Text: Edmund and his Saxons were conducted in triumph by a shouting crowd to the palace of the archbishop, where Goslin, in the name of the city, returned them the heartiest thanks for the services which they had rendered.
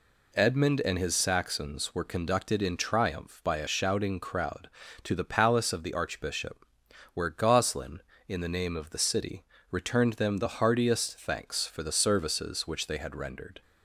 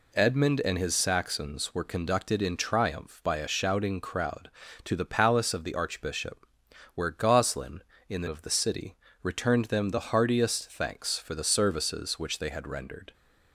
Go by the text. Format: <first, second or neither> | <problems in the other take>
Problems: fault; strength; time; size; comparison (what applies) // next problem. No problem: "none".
first | skips "name"; at 8.2 s